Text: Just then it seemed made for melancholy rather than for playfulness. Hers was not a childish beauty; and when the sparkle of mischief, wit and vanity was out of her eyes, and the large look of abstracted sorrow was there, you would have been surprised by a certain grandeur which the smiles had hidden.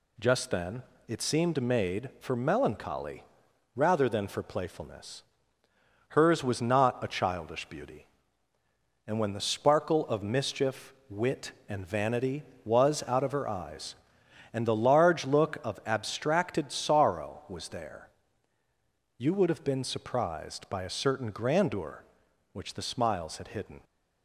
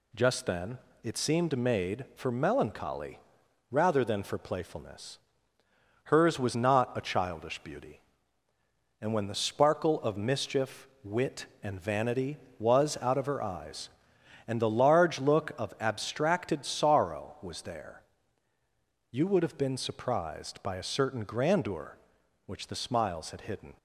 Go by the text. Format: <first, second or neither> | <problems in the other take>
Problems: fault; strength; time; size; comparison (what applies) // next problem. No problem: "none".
neither | pauses between "then" and "it"; slight; the same in both // pauses between "melancholy" and "rather"; noticeable; the same in both